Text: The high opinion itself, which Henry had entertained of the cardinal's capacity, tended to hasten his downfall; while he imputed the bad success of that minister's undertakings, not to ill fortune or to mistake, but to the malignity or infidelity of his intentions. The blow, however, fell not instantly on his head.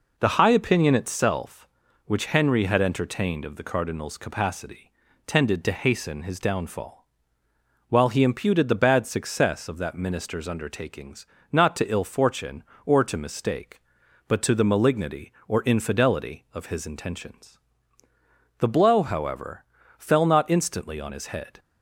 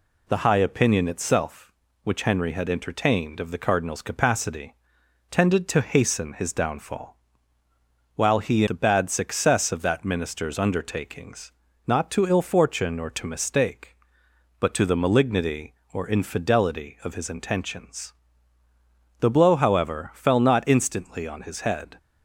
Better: first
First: none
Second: skips "imputed"; at 8.6 s

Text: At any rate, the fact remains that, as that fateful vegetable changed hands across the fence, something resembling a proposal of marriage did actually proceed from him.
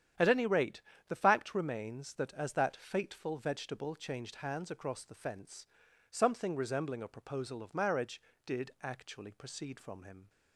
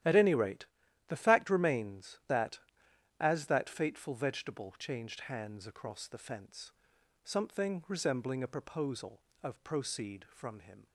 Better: first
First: starts louder than the rest; strong; until 1.4 s; 9.5 dB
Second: starts louder than the rest; strong; until 1.4 s; 12 dB // skips "marriage did actually"; at 9.6 s

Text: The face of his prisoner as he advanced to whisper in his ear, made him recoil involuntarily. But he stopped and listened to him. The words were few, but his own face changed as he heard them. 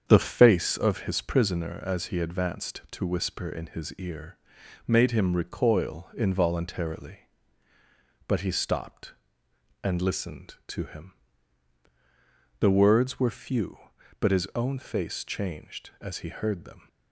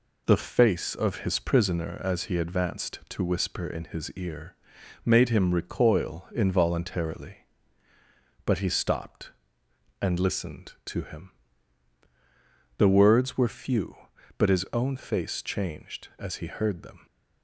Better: second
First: starts louder than the rest; strong; until 0.9 s; 7.5 dB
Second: none

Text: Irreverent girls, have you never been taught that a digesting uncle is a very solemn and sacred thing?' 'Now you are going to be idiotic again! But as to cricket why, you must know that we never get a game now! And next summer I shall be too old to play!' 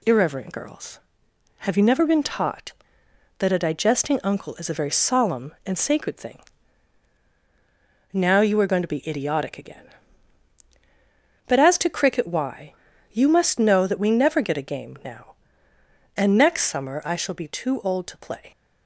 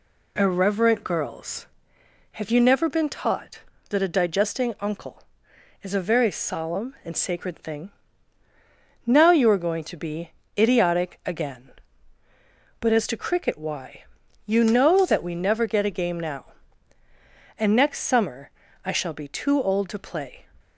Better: first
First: none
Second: pauses between "be" and "idiotic"; slight; at 10.3 s; 0.22 s long // skips "must"; at 14.6 s // pauses between "summer" and "I"; slight; at 18.5 s; 0.34 s long

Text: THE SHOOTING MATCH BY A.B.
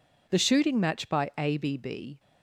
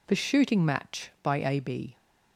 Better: second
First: goes on to say "B"; noticeable; from 1.5 s on; 0.62 s long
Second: none

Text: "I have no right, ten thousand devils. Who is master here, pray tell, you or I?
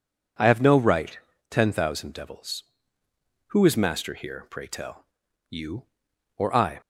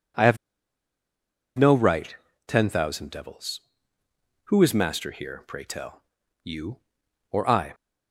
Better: first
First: none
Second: pauses between "have" and "no"; at 0.3 s; 1.2 s long

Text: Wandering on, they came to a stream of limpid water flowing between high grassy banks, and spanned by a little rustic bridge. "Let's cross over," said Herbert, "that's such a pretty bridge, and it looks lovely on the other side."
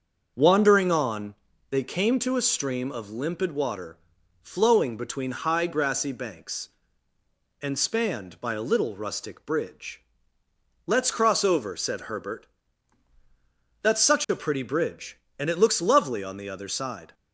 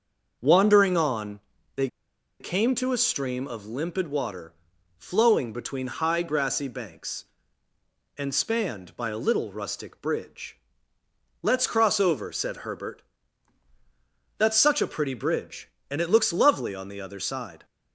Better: first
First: starts louder than the rest; until 1.3 s; 6.5 dB // pauses between "water" and "flowing"; at 3.9 s; 0.44 s long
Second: starts louder than the rest; until 1.4 s; 6.5 dB // pauses between "they" and "came"; noticeable; at 1.8 s; 0.51 s long // pauses between "water" and "flowing"; at 4.5 s; 0.44 s long

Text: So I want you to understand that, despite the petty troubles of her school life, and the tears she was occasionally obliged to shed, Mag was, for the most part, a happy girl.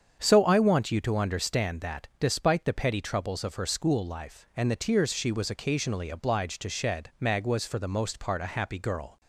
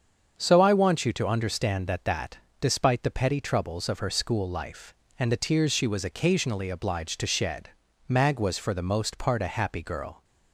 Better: first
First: starts louder than the rest; strong; until 1.2 s; 7.5 dB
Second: starts louder than the rest; strong; until 1.4 s; 7 dB // says "that" twice; at 2.0 s

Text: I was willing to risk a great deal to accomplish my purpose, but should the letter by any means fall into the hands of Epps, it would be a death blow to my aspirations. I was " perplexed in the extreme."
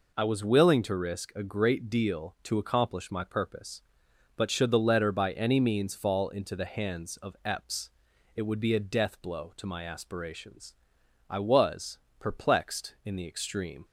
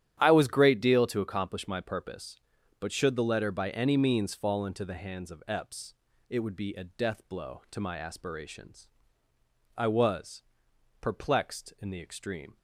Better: first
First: none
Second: starts louder than the rest; strong; until 1.2 s; 10.5 dB // skips "willing to risk a"; at 0.4 s

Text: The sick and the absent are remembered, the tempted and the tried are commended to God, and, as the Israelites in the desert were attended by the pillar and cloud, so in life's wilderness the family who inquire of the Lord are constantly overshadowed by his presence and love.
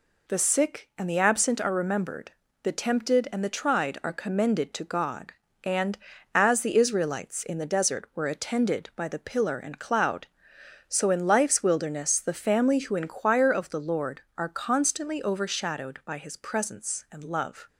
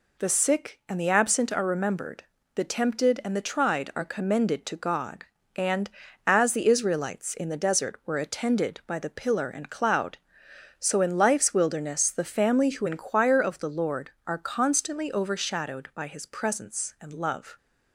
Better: neither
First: none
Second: none

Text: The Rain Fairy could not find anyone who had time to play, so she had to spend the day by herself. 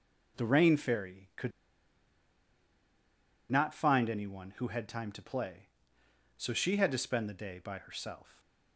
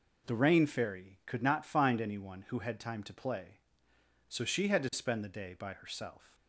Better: second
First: pauses between "could" and "not"; strong; at 1.5 s; 2.0 s long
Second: none

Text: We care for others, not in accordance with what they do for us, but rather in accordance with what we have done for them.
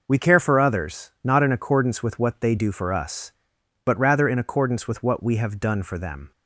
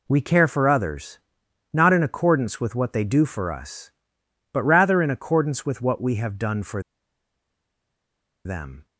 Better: first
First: none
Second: pauses between "for" and "them"; strong; at 6.8 s; 1.6 s long

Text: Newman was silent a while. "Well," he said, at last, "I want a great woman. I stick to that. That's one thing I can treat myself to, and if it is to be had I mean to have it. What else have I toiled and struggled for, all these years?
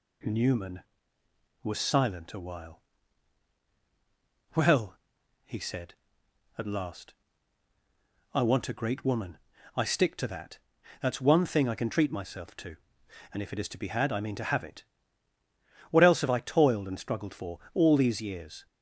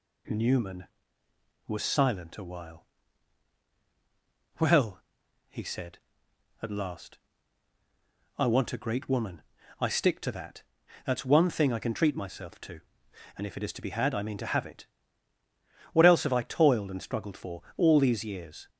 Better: neither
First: none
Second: none

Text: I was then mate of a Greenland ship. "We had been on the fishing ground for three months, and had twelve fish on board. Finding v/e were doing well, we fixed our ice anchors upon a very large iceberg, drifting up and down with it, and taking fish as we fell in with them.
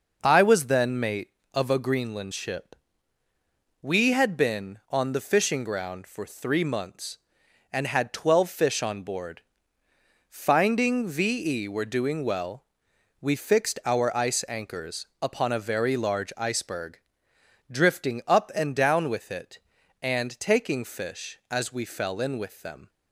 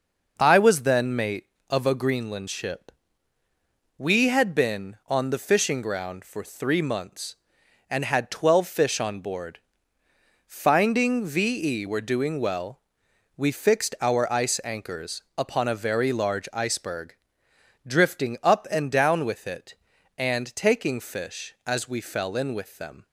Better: neither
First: pauses between "anchors" and "upon"; slight; at 15.0 s; 0.16 s long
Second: pauses between "anchors" and "upon"; slight; at 15.2 s; 0.16 s long

